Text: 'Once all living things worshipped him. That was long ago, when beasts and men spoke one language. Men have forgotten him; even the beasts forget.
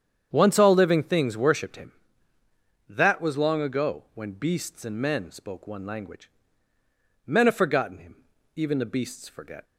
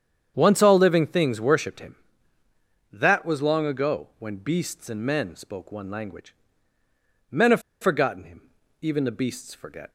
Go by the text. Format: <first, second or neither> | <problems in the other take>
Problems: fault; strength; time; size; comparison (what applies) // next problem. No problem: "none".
first | starts louder than the rest; strong; until 1.3 s; 8 dB; strong in the first // pauses between "have" and "forgotten"; slight; at 7.6 s; 0.20 s long